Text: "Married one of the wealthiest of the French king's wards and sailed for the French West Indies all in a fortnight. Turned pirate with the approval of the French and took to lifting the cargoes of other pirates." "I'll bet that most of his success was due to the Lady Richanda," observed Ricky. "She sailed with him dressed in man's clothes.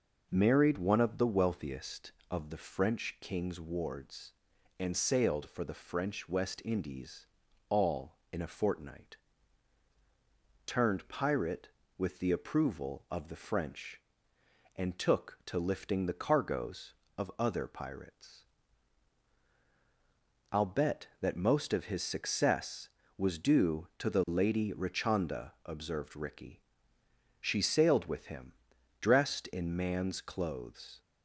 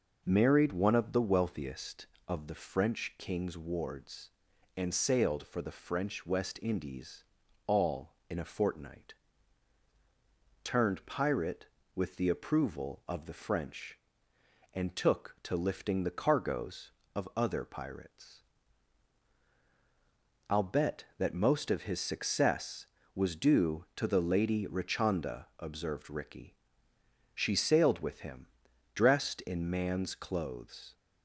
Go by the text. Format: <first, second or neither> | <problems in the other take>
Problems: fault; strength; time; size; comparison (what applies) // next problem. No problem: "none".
neither | pauses between "Indies" and "all"; the same in both // pauses between "him" and "dressed"; noticeable; the same in both